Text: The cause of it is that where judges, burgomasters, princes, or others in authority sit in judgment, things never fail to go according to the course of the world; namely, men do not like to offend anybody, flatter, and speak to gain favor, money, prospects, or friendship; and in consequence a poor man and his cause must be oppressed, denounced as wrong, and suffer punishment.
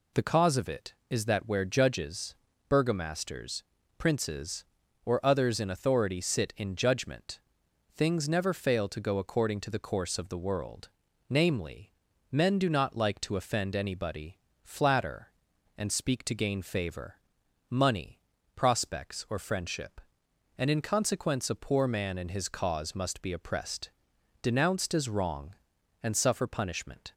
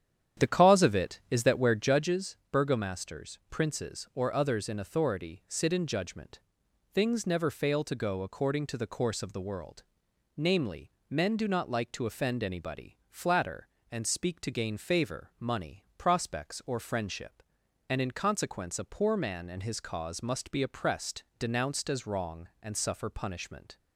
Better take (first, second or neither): first